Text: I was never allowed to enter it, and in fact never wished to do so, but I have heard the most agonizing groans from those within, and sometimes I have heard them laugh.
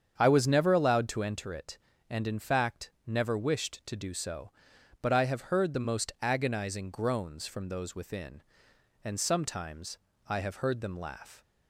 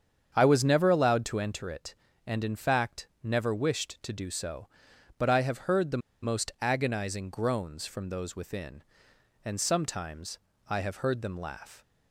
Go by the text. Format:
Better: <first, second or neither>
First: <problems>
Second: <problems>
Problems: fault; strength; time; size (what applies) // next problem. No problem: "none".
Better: first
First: starts louder than the rest; strong; until 1.1 s; 7.5 dB // pauses between "fact" and "never"; slight; at 2.8 s; 0.16 s long // pauses between "sometimes" and "I"; slight; at 9.9 s; 0.32 s long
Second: starts louder than the rest; strong; until 1.3 s; 7.5 dB // pauses between "fact" and "never"; slight; at 3.0 s; 0.16 s long // pauses between "the" and "most"; slight; at 5.9 s; 0.24 s long // pauses between "sometimes" and "I"; slight; at 10.3 s; 0.32 s long